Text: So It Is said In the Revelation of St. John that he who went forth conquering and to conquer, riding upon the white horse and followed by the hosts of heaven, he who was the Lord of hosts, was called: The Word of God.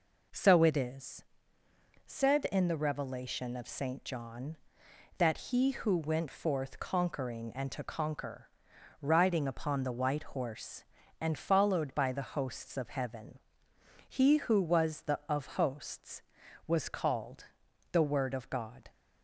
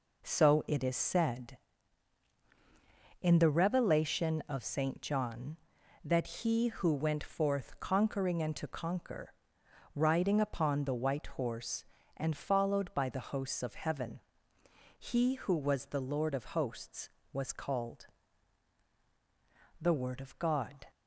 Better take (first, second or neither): second